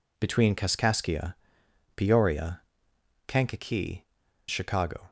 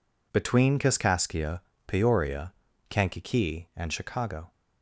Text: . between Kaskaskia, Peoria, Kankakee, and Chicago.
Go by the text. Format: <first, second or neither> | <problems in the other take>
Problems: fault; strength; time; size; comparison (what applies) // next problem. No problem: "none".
second | skips "and"; at 4.2 s